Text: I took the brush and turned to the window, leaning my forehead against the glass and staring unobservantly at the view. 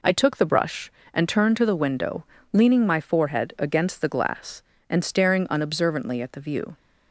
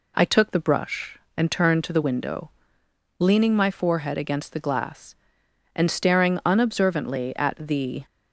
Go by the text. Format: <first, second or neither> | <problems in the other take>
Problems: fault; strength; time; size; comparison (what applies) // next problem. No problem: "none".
first | stops before "view"; at 8.0 s